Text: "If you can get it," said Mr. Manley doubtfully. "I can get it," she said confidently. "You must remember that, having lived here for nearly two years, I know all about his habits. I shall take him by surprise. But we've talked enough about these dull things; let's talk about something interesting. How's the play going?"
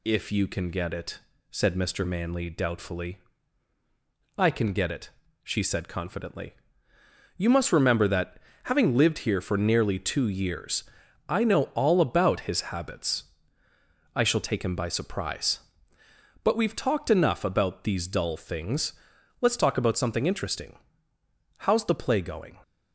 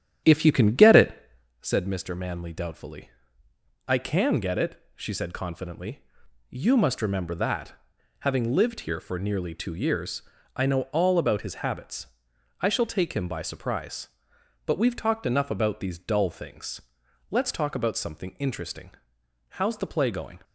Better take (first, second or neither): first